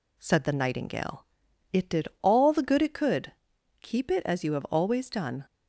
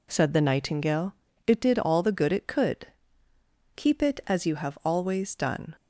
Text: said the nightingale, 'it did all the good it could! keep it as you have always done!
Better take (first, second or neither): neither